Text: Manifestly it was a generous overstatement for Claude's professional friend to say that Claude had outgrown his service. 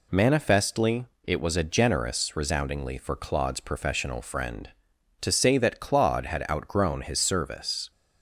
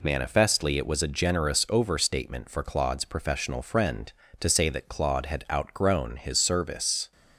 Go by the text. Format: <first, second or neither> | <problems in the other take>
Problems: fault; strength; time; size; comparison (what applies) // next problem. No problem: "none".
second | pauses between "Manifestly" and "it"; slight; at 1.0 s; 0.20 s long // says "resoundingly" for "overstatement"; at 2.3 s